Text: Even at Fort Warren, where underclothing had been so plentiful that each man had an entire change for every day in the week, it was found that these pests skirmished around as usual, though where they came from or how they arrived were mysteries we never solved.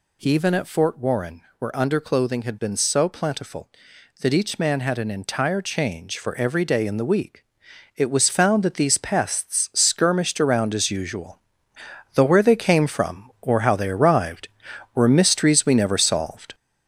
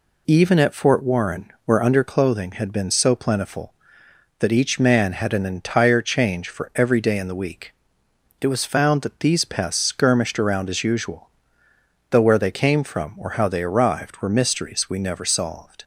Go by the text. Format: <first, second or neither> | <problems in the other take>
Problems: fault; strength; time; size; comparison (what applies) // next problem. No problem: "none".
second | gets louder; noticeable; throughout; 5 dB